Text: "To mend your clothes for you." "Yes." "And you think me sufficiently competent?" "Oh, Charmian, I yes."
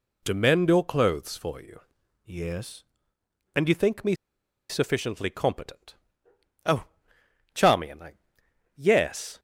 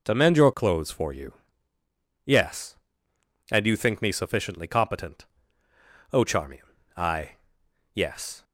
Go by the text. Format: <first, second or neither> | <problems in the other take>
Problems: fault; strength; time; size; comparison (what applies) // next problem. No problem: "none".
second | pauses between "me" and "sufficiently"; noticeable; at 4.1 s; 0.55 s long // pauses between "I" and "yes"; noticeable; at 8.1 s; 0.62 s long; noticeable in the second